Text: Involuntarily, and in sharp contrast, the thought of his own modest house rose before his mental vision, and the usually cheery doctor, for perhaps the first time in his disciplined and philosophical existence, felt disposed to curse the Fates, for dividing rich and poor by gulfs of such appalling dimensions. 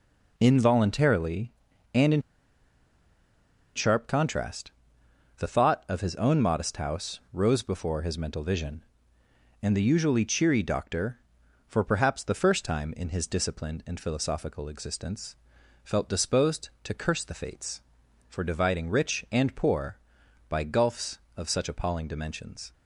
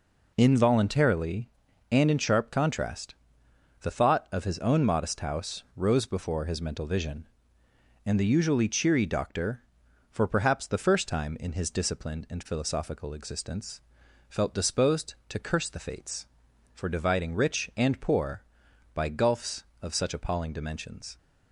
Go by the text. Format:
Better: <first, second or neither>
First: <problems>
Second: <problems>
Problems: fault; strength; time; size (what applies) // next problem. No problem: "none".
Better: second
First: pauses between "in" and "sharp"; strong; at 2.2 s; 1.5 s long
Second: none